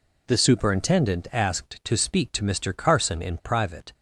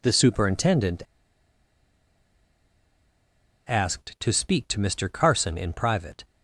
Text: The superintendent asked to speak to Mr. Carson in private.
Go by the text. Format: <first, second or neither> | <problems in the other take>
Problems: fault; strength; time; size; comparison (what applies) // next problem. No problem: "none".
first | pauses between "superintendent" and "asked"; strong; at 1.0 s; 2.6 s long